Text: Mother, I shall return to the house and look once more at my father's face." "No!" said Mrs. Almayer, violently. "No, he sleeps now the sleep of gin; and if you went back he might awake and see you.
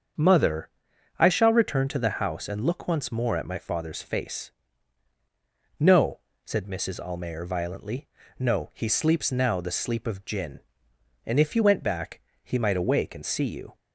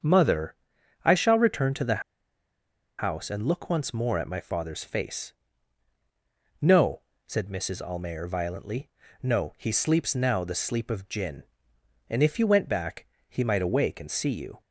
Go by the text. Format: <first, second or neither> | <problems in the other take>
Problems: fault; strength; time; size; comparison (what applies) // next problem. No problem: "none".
first | starts louder than the rest; strong; until 1.5 s; 7 dB; strong in the first // pauses between "the" and "house"; noticeable; at 2.0 s; 0.96 s long // pauses between "back" and "he"; slight; at 13.0 s; 0.22 s long; slight in the first